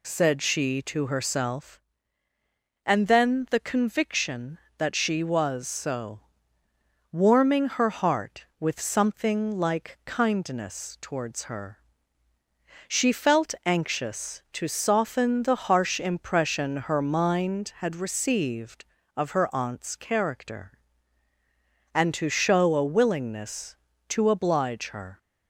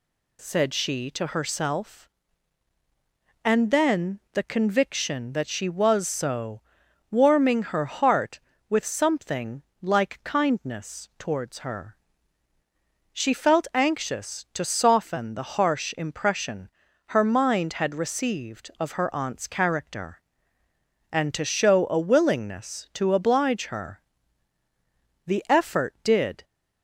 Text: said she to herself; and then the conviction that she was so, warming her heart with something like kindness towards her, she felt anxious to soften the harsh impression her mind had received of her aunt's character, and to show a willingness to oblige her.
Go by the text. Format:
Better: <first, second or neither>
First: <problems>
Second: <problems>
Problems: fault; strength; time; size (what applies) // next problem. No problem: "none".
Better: first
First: none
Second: pauses between "something" and "like"; slight; at 9.6 s; 0.20 s long // pauses between "impression" and "her"; at 16.6 s; 0.38 s long // goes on to say "The effort did"; noticeable; from 25.2 s on; 1.1 s long